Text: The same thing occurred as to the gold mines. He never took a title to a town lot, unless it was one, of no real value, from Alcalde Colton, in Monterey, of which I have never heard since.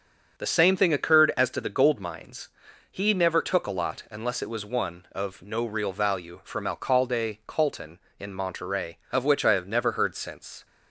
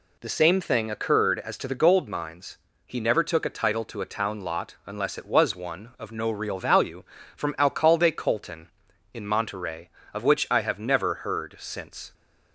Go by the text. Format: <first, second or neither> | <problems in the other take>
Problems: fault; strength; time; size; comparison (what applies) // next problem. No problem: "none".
second | starts louder than the rest; strong; until 1.4 s; 7 dB // skips "title to a town"; at 3.7 s